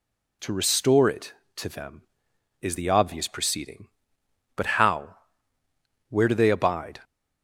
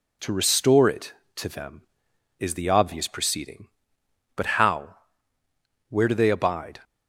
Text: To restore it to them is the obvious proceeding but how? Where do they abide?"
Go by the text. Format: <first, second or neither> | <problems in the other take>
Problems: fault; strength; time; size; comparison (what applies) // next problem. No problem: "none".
first | gets quieter; slight; throughout; 2 dB